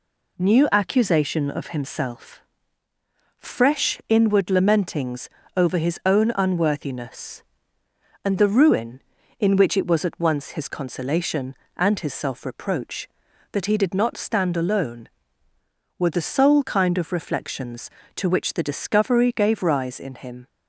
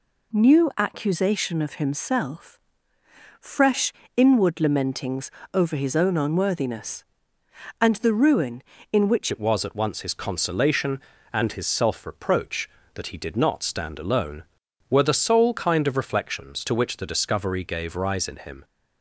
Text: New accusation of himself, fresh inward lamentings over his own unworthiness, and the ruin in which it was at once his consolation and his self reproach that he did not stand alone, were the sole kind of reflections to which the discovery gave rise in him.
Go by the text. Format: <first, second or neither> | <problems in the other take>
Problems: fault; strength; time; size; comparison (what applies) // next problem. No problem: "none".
first | pauses between "fresh" and "inward"; slight; at 3.9 s; 0.24 s long // pauses between "lamentings" and "over"; slight; at 5.2 s; 0.24 s long; slight in the first // changes voice at "it"; from 9.3 s on; 9.3 s long